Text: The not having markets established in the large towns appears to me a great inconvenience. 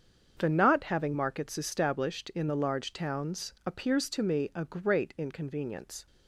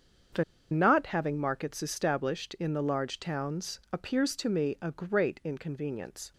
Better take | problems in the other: first | starts louder than the rest; strong; until 1.6 s; 7.5 dB; strong in the first // pauses between "The" and "not"; slight; at 0.4 s; 0.27 s long

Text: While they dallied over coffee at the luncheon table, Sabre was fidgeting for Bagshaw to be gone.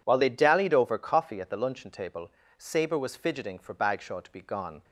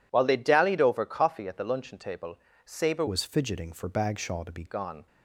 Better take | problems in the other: first | changes voice from "was" to "be"; from 3.0 to 4.6 s; 1.6 s long

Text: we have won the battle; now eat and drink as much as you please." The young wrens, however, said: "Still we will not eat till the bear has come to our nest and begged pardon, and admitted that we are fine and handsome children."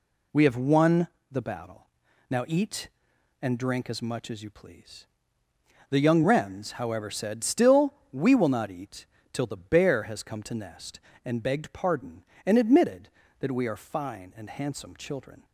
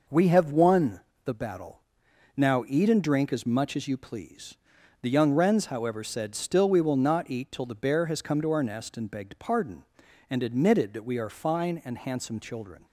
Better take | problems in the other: second | pauses between "won" and "the"; slight; at 1.0 s; 0.24 s long; slight in the second // pauses between "Still" and "we"; slight; at 7.9 s; 0.18 s long // pauses between "eat" and "till"; slight; at 9.0 s; 0.26 s long // skips "our"; at 10.5 s

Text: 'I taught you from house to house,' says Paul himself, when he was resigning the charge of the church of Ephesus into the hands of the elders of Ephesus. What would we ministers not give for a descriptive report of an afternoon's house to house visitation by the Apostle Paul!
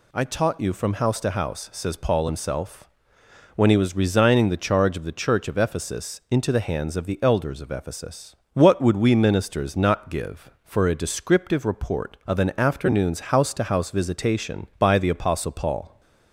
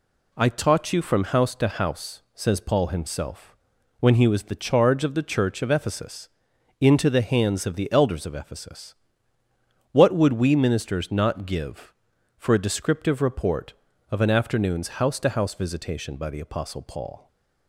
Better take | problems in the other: first | skips "resigning"; at 4.4 s // pauses between "Ephesus" and "into"; noticeable; at 6.2 s; 0.50 s long // stays silent after the last word; slight; from 17.1 s on; 0.5 s long

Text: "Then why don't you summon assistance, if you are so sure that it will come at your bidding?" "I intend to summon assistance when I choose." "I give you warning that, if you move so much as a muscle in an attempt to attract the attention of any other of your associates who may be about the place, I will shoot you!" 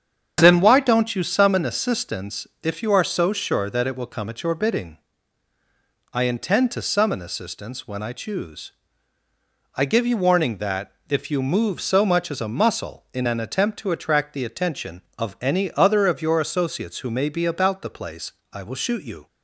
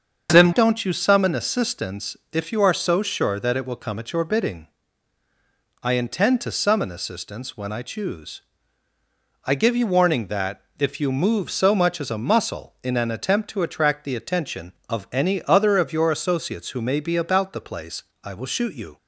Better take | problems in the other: first | starts louder than the rest; until 1.3 s; 7 dB; strong in the first // skips "why"; at 0.5 s

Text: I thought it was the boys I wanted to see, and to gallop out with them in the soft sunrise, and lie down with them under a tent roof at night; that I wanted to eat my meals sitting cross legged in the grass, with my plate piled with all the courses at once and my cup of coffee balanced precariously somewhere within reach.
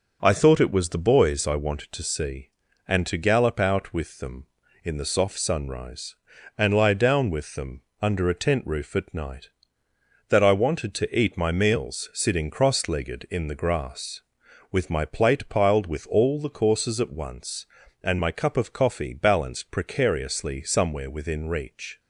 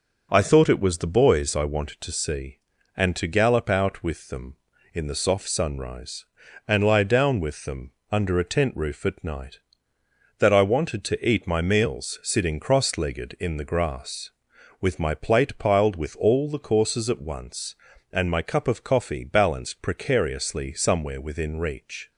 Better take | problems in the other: neither | pauses between "them" and "under"; slight; the same in both

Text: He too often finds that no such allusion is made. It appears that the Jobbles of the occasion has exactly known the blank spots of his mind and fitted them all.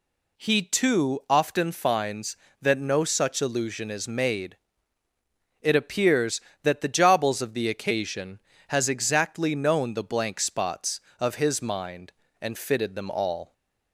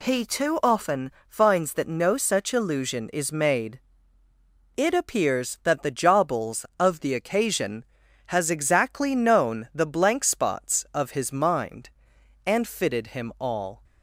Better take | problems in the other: first | pauses between "often" and "finds"; slight; at 1.1 s; 0.16 s long // says "him" for "them"; at 13.1 s

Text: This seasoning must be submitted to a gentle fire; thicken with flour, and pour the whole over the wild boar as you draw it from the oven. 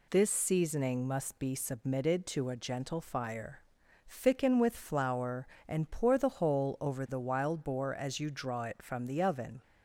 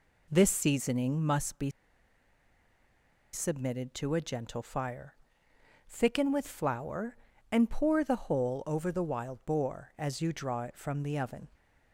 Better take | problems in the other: first | pauses between "be" and "submitted"; strong; at 1.7 s; 1.6 s long

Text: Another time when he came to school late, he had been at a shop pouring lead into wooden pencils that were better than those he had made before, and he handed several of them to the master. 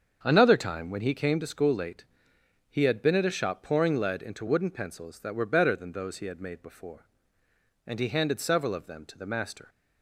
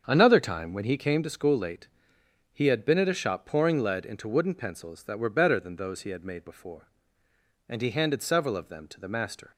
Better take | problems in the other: neither | starts louder than the rest; strong; the same in both

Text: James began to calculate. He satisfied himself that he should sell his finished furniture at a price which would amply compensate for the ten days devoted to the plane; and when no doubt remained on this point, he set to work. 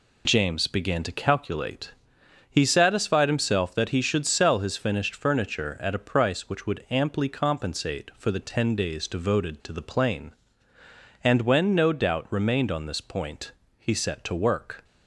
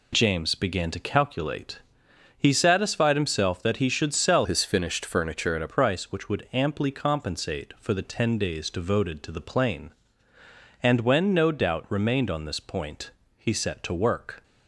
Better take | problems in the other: first | changes voice from "his" to "a"; from 4.4 to 5.6 s; 1.2 s long

